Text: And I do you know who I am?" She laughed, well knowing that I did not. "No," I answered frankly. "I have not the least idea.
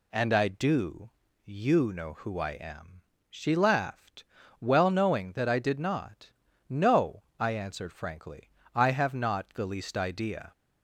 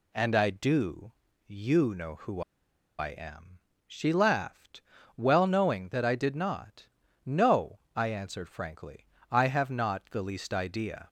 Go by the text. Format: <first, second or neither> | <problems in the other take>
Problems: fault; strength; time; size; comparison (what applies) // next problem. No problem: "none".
first | pauses between "do" and "you"; slight; at 1.1 s; 0.34 s long; slight in the first // pauses between "who" and "I"; noticeable; at 2.4 s; 0.56 s long